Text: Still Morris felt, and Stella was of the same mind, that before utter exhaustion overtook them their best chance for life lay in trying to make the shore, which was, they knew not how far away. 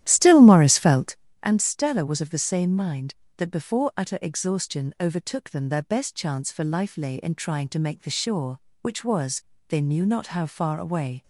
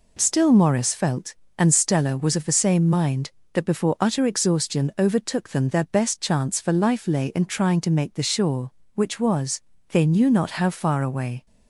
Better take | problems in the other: second | starts louder than the rest; strong; until 1.3 s; 12.5 dB

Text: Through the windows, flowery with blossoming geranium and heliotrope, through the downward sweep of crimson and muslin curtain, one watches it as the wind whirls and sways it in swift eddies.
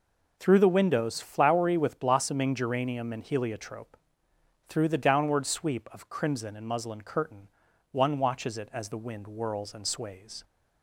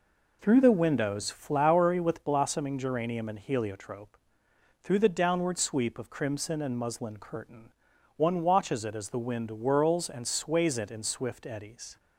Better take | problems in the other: second | stops before "it in swift eddies"; at 10.4 s

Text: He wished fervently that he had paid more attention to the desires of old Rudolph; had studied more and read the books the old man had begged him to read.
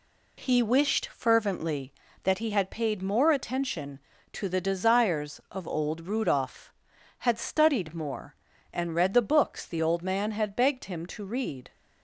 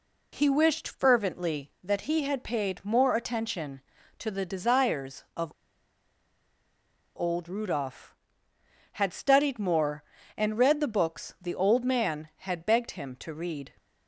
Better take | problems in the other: first | pauses between "of" and "old"; strong; at 5.5 s; 1.6 s long

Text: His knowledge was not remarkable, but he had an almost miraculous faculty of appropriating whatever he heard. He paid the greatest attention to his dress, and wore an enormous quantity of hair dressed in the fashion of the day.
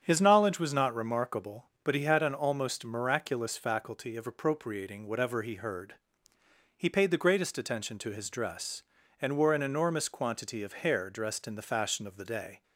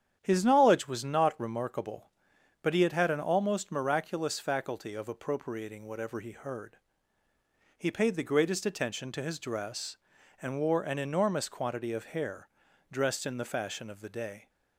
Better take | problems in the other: first | starts louder than the rest; strong; until 1.2 s; 9 dB; strong in the first // says "had" twice; at 2.9 s // pauses between "hair" and "dressed"; at 12.4 s; 0.42 s long

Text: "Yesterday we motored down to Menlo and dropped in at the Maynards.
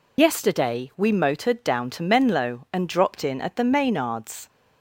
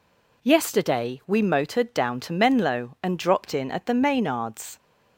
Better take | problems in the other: second | loses the start of "Yesterday"; at 0.1 s; 65 ms

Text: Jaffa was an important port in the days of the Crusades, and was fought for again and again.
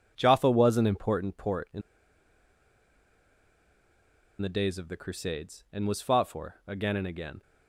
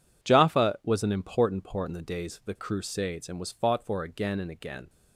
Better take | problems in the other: second | pauses between "in" and "the"; strong; at 1.8 s; 2.6 s long

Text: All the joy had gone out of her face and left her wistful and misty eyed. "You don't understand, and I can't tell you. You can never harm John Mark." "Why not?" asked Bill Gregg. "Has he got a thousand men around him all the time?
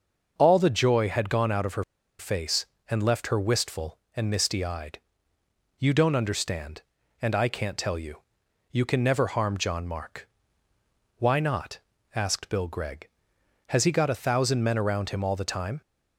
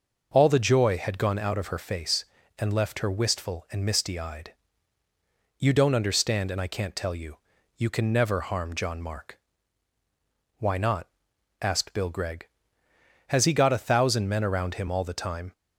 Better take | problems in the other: second | starts louder than the rest; until 1.3 s; 6 dB // pauses between "her" and "face"; slight; at 1.8 s; 0.35 s long

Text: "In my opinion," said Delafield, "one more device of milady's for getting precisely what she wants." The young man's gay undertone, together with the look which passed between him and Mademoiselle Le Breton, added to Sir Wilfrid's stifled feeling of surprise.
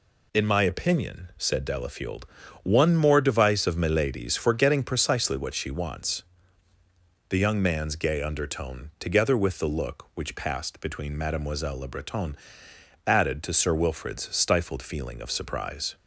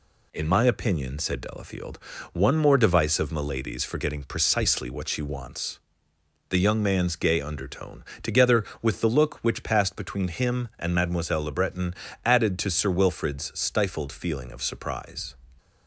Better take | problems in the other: second | skips "him and"; at 11.1 s

